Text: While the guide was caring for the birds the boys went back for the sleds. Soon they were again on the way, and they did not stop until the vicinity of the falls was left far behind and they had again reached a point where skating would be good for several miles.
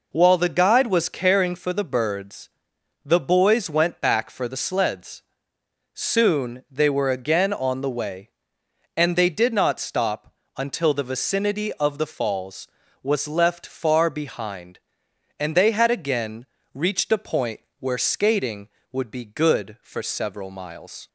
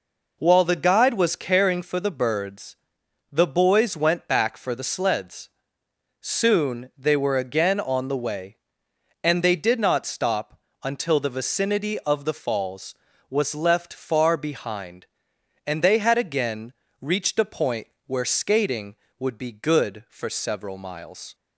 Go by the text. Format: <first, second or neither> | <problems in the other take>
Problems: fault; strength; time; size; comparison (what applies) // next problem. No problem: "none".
neither | pauses between "birds" and "the"; noticeable; the same in both // pauses between "stop" and "until"; slight; the same in both // pauses between "again" and "reached"; slight; the same in both // pauses between "point" and "where"; slight; the same in both